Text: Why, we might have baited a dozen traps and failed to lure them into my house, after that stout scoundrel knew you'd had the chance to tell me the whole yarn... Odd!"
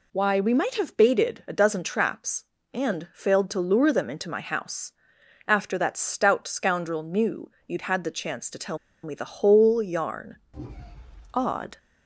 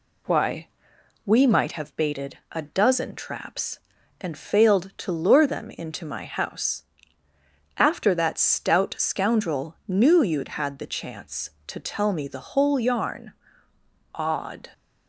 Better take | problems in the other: second | pauses between "knew" and "you'd"; slight; at 7.4 s; 0.18 s long // pauses between "tell" and "me"; slight; at 8.7 s; 0.25 s long

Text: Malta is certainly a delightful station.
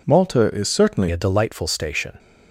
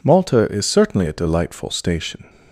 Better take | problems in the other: second | changes voice at "a"; from 1.1 s on; 1.0 s long

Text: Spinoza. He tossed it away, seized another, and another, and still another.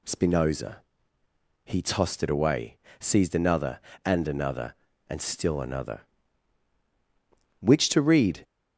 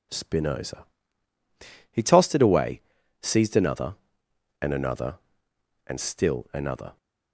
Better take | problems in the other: second | goes on to say "Which to read"; noticeable; from 7.6 s on; 0.82 s long

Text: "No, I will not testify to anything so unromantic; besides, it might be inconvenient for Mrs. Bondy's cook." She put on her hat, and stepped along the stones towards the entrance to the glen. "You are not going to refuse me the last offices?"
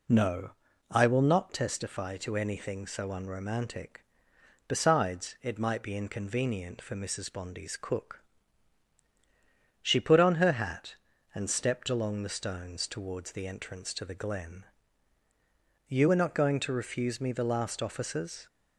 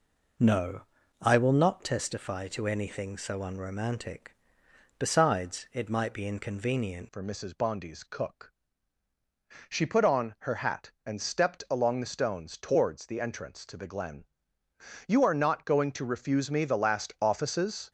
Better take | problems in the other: first | changes voice at "for"; from 7.1 s on; 10.8 s long

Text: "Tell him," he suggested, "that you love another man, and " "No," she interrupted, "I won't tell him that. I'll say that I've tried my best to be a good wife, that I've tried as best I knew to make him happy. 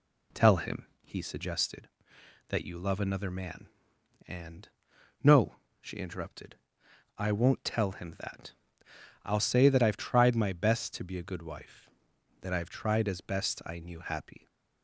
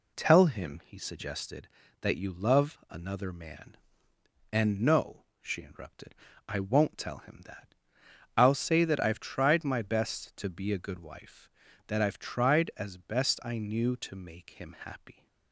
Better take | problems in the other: second | skips "to make him"; at 13.9 s

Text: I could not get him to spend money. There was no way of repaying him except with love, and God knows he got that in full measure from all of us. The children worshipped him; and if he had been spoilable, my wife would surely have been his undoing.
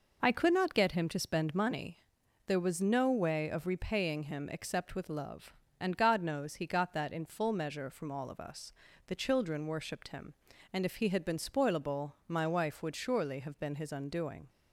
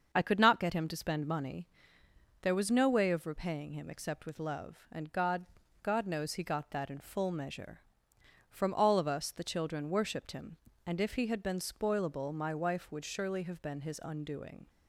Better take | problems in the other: first | starts louder than the rest; until 1.1 s; 6.5 dB // says "God" twice; at 5.8 s

